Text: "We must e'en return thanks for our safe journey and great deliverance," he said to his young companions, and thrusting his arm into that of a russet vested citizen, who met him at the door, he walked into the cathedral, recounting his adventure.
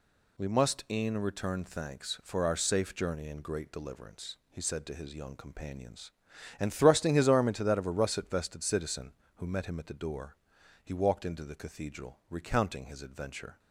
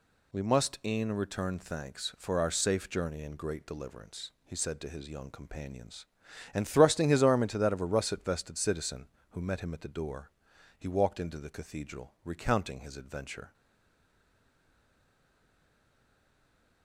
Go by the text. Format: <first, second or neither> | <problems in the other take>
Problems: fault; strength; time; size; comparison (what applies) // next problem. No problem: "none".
first | stays silent after the last word; strong; from 13.5 s on; 3.3 s long